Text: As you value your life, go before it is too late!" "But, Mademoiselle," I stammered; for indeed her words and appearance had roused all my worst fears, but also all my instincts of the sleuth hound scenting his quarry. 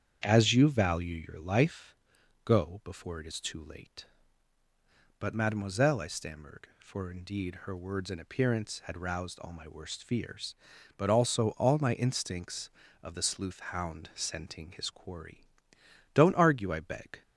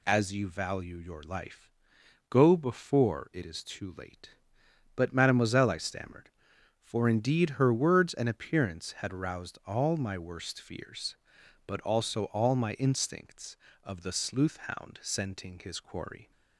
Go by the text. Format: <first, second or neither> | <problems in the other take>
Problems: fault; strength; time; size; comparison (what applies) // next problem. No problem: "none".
second | starts louder than the rest; strong; until 1.2 s; 8 dB // pauses between "sleuth" and "hound"; slight; at 13.5 s; 0.16 s long // goes on to say "Don't argue I beg"; noticeable; from 16.1 s on; 1.0 s long